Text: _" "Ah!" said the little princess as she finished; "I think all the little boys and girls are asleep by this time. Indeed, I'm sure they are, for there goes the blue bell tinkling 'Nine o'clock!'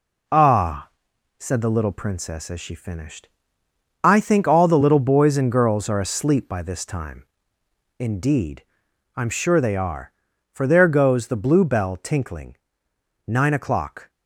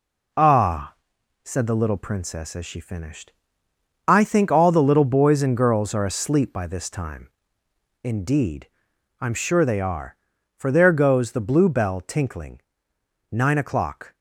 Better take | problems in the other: neither | pauses between "tinkling" and "Nine"; noticeable; the same in both

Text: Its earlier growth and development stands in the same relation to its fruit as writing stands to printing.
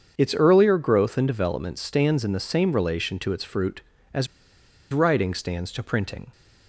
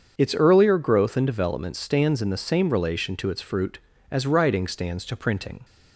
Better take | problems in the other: second | starts louder than the rest; until 1.1 s; 7 dB; also in the second // pauses between "as" and "writing"; noticeable; at 4.2 s; 0.66 s long

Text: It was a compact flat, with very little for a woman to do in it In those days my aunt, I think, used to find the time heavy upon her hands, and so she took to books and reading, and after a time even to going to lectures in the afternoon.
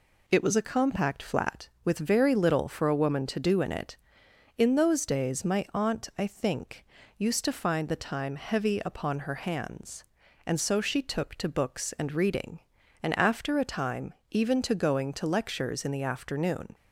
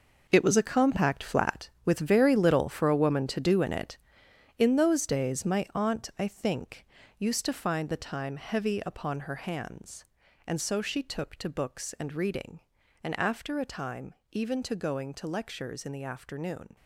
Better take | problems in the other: first | gets quieter; strong; throughout; 11.5 dB // pauses between "time" and "even"; slight; at 14.1 s; 0.16 s long; slight in the first

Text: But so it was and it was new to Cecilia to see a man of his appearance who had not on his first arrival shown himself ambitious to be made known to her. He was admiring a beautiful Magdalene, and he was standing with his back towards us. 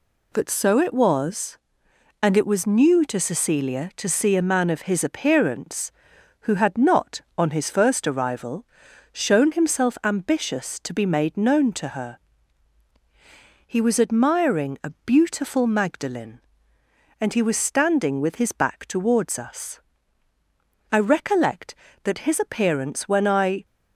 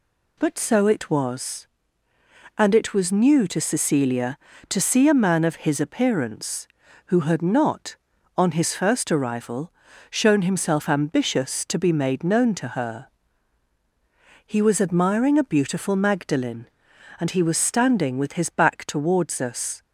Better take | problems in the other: second | pauses between "arrival" and "shown"; noticeable; at 8.6 s; 0.46 s long; also in the second // pauses between "a" and "beautiful"; slight; at 14.9 s; 0.16 s long // goes on to say "I recollect that his appearance when I"; strong; from 20.9 s on; 2.7 s long

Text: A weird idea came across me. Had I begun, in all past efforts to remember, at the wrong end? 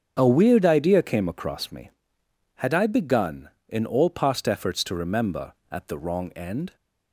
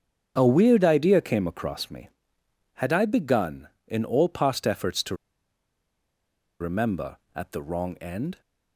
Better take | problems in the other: first | starts louder than the rest; strong; until 1.3 s; 7.5 dB; strong in the first // pauses between "to" and "remember"; strong; at 5.1 s; 1.4 s long

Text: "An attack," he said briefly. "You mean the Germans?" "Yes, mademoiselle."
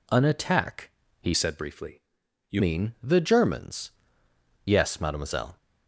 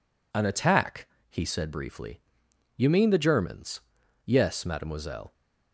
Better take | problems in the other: second | changes voice from "said" to "You"; from 1.3 to 2.6 s; 1.3 s long

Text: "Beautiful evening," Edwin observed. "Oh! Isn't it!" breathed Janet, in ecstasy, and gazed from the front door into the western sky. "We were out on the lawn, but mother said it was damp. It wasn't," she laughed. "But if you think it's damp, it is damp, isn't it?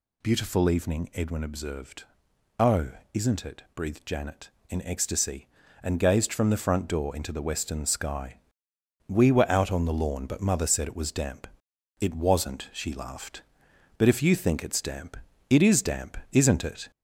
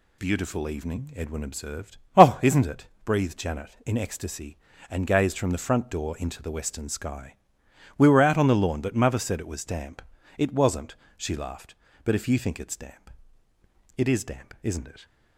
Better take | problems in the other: second | gets louder; slight; throughout; 2.5 dB

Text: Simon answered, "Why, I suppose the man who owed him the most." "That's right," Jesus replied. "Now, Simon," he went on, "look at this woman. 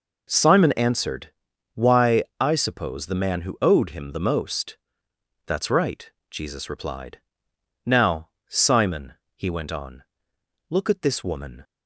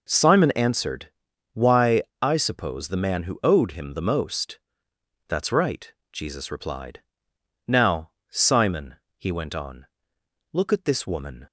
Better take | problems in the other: neither | none

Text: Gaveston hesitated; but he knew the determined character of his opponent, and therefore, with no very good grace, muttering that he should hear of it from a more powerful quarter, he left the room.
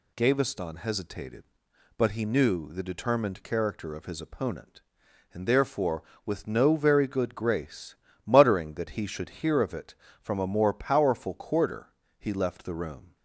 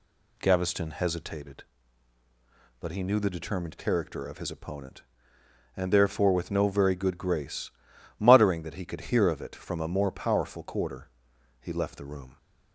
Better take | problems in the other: first | says "could" for "should"; at 8.8 s

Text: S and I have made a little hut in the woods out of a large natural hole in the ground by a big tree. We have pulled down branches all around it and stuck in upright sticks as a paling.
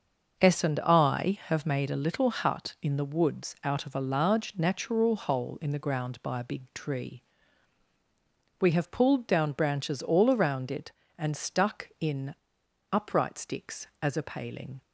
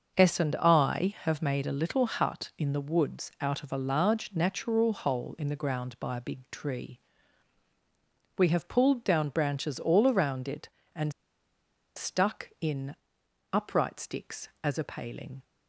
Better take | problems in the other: first | starts louder than the rest; until 1.2 s; 6 dB; also in the first // pauses between "and" and "stuck"; noticeable; at 11.1 s; 0.84 s long // pauses between "in" and "upright"; noticeable; at 12.9 s; 0.58 s long; noticeable in the first

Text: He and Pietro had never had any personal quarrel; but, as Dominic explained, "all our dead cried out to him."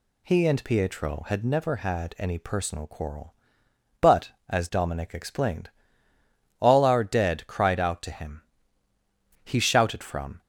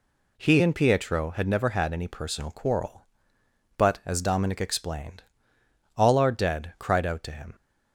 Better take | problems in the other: second | goes on to say "He shouted from"; noticeable; from 9.4 s on; 0.96 s long

